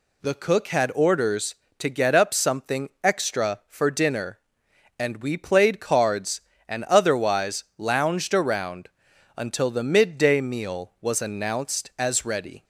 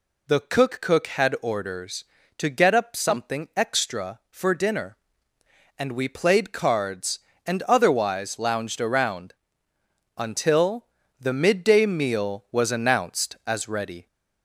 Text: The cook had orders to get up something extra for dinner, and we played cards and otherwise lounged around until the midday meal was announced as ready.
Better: first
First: pauses between "around" and "until"; noticeable; at 8.8 s; 0.48 s long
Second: says "cook" twice; at 0.8 s // pauses between "around" and "until"; noticeable; at 9.3 s; 0.84 s long // pauses between "until" and "the"; slight; at 10.8 s; 0.32 s long

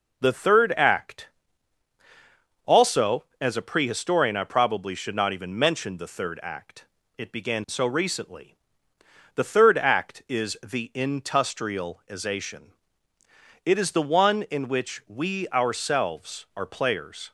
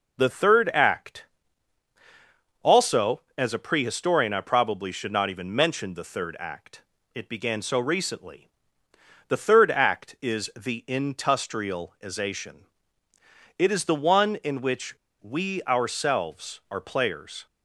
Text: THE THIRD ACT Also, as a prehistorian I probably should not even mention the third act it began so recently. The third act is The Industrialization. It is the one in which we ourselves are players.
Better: first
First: pauses between "ACT" and "Also"; strong; at 1.2 s; 1.3 s long // pauses between "act" and "it"; slight; at 6.8 s; 0.32 s long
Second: pauses between "ACT" and "Also"; strong; at 1.2 s; 1.3 s long // pauses between "act" and "it"; slight; at 6.8 s; 0.32 s long // pauses between "which" and "we"; slight; at 14.9 s; 0.27 s long

